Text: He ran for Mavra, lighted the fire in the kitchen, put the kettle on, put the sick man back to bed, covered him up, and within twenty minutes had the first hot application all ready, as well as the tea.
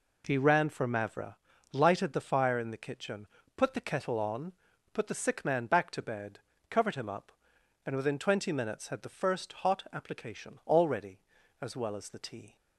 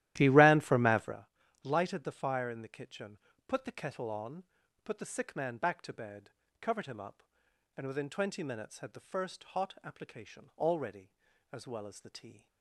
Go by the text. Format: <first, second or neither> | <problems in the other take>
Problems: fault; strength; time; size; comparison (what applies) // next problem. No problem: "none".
first | starts louder than the rest; strong; until 1.1 s; 14 dB